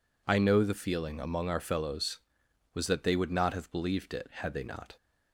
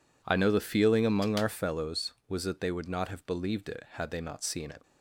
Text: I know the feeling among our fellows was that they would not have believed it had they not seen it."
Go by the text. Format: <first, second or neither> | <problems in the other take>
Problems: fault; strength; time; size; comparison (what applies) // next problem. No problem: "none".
second | stops before "seen it"; at 4.9 s